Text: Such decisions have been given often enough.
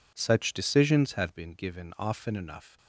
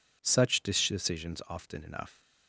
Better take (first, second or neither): first